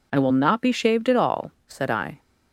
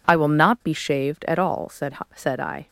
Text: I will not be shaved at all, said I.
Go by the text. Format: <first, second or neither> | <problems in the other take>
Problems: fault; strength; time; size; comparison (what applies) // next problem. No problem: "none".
first | says "said" twice; at 2.1 s